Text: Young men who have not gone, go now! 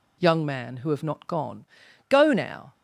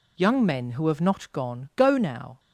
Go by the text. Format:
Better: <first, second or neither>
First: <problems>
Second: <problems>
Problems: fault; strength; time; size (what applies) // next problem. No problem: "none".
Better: second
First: says "man" for "men"; at 0.4 s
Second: none